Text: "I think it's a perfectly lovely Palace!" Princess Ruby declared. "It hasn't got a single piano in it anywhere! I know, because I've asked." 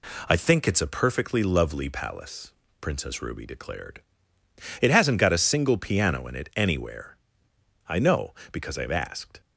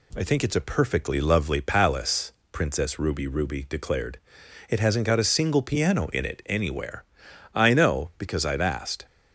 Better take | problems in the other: first | says "Ruby" twice; at 3.2 s

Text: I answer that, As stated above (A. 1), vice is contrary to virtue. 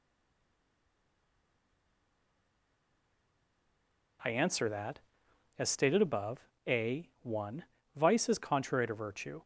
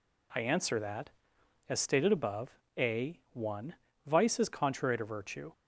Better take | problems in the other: second | stays silent before the first word; strong; until 4.1 s; 4.1 s long

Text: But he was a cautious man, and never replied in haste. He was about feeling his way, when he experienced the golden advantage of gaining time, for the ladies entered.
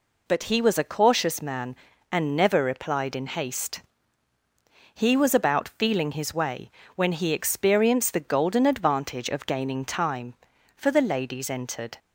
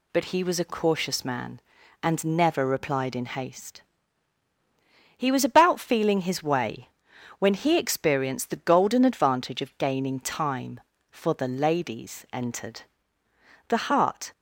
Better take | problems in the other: first | goes on to say "The heart"; noticeable; from 13.6 s on; 0.64 s long

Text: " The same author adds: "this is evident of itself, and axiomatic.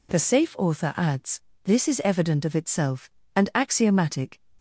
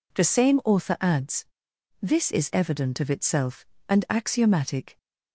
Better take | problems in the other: second | says "safe" for "same"; at 0.1 s

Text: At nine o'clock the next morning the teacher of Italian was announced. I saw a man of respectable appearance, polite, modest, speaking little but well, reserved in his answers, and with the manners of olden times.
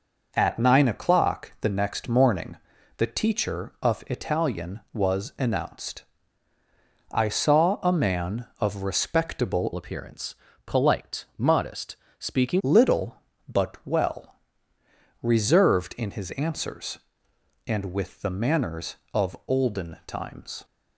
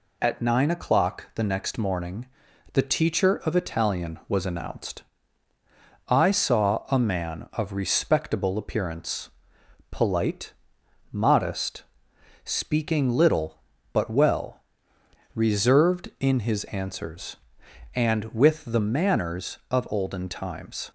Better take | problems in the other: second | pauses between "morning" and "the"; at 2.5 s; 0.44 s long; noticeable in the second // changes voice from "appearance" to "speaking"; from 9.7 to 12.6 s; 2.9 s long

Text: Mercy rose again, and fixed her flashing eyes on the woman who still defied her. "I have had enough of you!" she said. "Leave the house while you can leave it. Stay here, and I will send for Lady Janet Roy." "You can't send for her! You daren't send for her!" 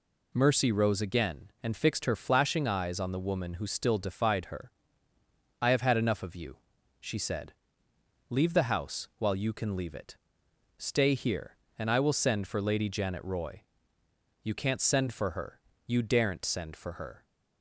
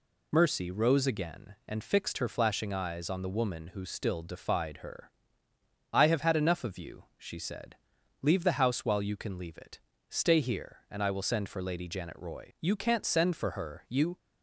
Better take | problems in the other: first | stops before "daren't send for her"; at 14.1 s

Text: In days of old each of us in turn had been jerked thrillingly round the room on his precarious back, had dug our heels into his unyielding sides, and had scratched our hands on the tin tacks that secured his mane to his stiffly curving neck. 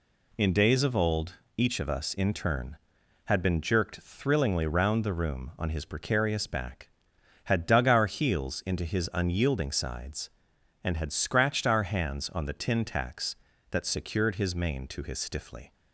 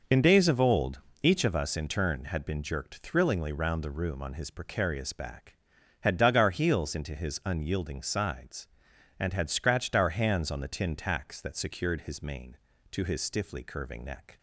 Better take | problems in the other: second | pauses between "old" and "each"; slight; at 1.3 s; 0.24 s long; slight in the second // stops before "curving neck"; at 15.7 s

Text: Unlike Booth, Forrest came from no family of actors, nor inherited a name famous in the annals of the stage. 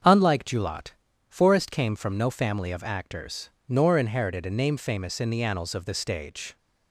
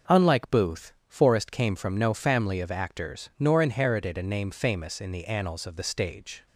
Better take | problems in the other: second | starts louder than the rest; until 1.4 s; 7 dB // says "Julot" for "Booth"; at 0.4 s

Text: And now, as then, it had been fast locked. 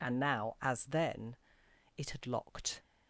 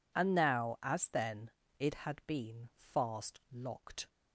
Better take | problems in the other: second | skips "been fast"; at 2.2 s

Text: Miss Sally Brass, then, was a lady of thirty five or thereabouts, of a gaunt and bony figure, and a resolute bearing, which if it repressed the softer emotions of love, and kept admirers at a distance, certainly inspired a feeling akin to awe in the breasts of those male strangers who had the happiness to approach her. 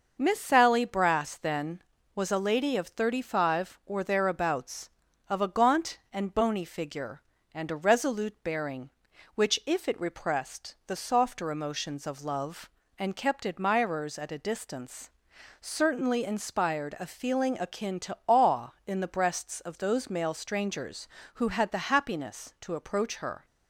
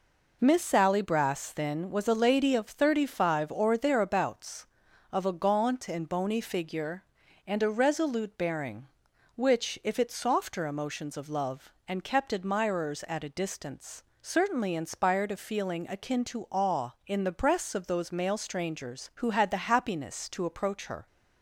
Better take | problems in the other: first | skips "repressed the"; at 10.0 s

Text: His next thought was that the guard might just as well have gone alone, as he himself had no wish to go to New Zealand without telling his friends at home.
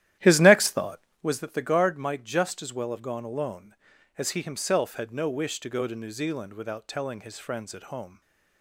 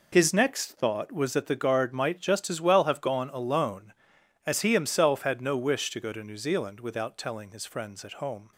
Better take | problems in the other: second | starts louder than the rest; strong; until 1.3 s; 12.5 dB // stays silent after the last word; slight; from 8.0 s on; 0.6 s long

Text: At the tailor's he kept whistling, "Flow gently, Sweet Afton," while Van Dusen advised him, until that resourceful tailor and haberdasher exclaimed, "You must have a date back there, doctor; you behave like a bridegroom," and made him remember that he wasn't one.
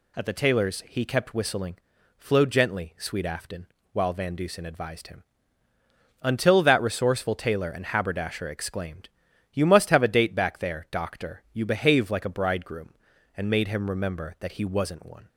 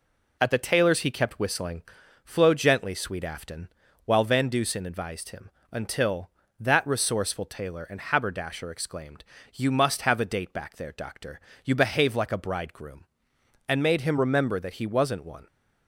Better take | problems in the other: neither | none

